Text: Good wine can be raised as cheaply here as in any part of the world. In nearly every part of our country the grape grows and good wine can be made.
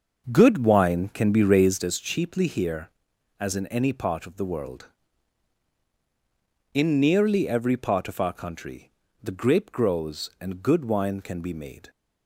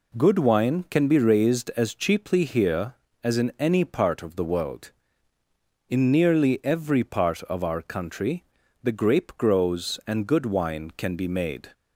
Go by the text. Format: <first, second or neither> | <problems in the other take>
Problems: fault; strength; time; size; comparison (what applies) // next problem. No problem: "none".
second | starts louder than the rest; until 1.9 s; 6 dB // pauses between "country" and "the"; slight; at 8.8 s; 0.32 s long; also in the second